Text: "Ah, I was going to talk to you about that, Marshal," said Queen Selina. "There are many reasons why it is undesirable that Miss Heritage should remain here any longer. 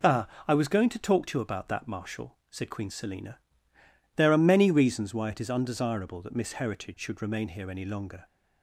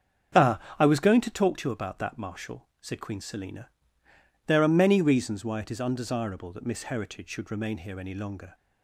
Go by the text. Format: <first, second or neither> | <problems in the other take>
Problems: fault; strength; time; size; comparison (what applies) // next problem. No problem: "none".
first | starts louder than the rest; strong; until 1.4 s; 7.5 dB